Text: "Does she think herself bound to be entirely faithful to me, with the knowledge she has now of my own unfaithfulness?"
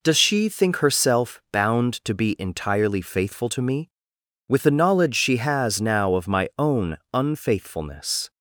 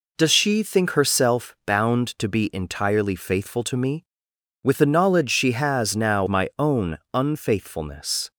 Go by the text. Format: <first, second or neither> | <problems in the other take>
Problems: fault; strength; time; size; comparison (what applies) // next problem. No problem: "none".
first | skips "of"; at 6.2 s // pauses between "own" and "unfaithfulness"; slight; at 6.9 s; 0.16 s long; slight in the first